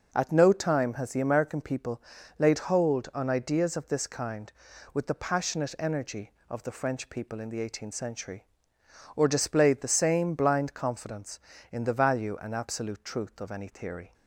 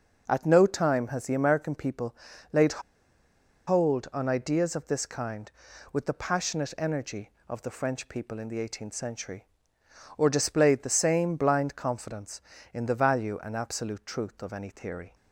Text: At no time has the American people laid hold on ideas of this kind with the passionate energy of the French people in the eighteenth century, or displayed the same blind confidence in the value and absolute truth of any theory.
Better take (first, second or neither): first